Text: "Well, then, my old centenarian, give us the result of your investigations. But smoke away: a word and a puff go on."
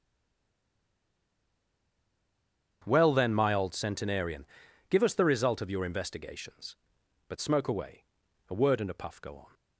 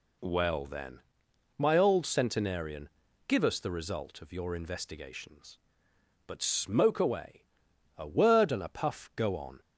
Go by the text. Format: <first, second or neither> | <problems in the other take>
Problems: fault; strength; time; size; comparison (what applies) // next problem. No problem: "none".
second | stays silent before the first word; strong; until 2.8 s; 2.8 s long // starts louder than the rest; strong; until 3.8 s; 8 dB